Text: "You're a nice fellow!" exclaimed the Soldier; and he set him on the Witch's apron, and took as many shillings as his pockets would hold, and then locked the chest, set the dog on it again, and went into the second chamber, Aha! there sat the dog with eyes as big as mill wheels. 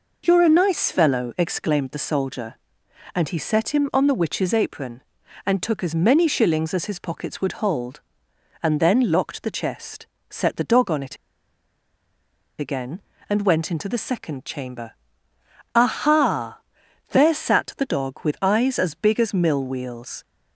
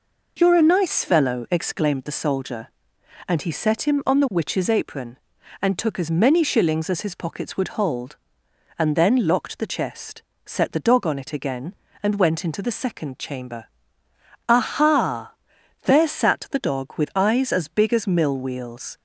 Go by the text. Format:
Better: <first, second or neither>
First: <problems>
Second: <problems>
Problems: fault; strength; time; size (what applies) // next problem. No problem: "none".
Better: second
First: pauses between "it" and "again"; strong; at 11.1 s; 1.4 s long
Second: none